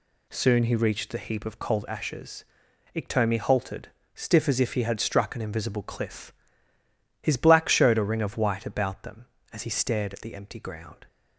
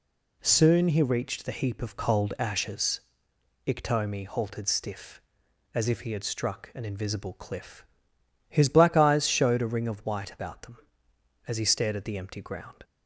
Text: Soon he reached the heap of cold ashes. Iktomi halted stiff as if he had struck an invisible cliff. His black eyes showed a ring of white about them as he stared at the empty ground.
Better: second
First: pauses between "halted" and "stiff"; slight; at 3.8 s; 0.26 s long // skips "eyes"; at 7.6 s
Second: none

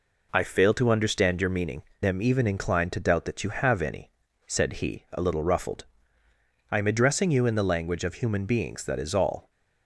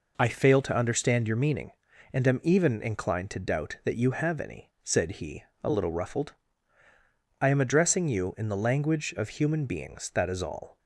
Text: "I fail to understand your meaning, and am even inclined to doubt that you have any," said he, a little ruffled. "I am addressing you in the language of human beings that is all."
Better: second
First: skips "and"; at 1.9 s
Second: none

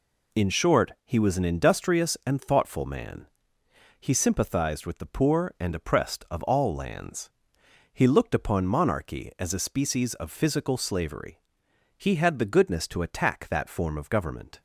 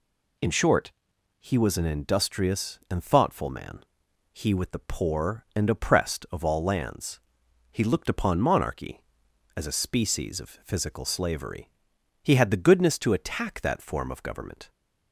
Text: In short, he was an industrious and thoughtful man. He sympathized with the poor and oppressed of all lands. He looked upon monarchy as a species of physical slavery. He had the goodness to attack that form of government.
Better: first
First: none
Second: skips "sympathized"; at 4.5 s

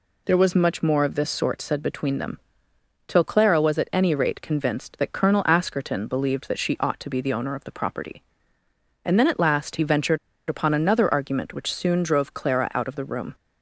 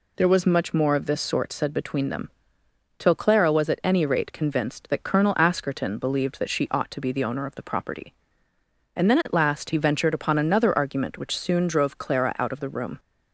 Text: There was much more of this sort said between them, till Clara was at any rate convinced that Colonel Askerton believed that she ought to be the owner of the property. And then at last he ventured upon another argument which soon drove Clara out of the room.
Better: second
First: pauses between "ventured" and "upon"; slight; at 10.1 s; 0.31 s long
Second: none

